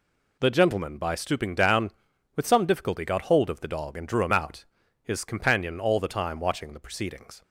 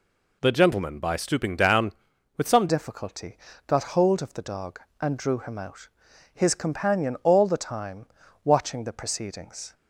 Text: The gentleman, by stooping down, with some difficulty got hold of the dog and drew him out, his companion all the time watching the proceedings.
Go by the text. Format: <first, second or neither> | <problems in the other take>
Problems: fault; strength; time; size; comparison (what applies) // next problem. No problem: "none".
first | changes voice at "difficulty"; from 2.6 s on; 7.1 s long // pauses between "difficulty" and "got"; slight; at 3.3 s; 0.28 s long // pauses between "time" and "watching"; at 8.0 s; 0.38 s long